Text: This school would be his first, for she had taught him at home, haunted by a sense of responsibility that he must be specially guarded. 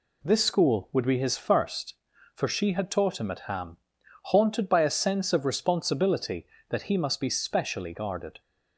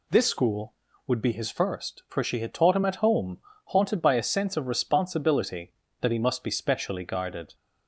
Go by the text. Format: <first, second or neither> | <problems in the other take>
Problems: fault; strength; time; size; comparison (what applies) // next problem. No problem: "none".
second | says "ham" for "home"; at 3.4 s